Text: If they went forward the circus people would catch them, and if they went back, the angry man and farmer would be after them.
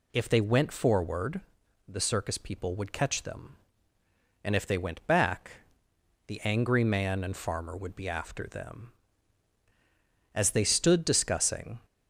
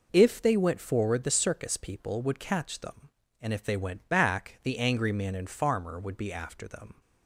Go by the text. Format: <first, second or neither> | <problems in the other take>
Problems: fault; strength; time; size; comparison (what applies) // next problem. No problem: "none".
second | pauses between "forward" and "the"; noticeable; at 1.3 s; 0.50 s long // goes on to say "As they stood discussing"; from 10.3 s on; 1.4 s long